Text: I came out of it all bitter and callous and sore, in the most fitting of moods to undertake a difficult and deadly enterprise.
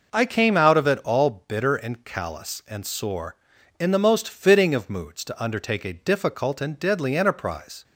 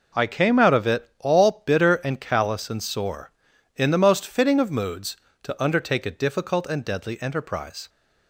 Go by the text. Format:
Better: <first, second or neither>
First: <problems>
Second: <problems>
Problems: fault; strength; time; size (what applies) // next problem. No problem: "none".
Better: neither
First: none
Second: none